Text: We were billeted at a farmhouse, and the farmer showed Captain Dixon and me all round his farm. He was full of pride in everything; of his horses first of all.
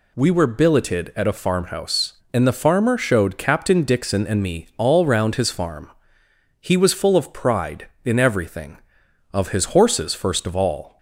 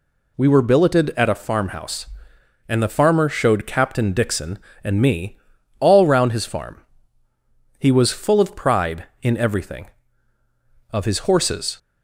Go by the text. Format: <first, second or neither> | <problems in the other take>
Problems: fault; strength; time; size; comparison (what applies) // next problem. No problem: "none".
first | pauses between "me" and "all"; at 5.3 s; 0.42 s long // stops before "first of all"; at 11.7 s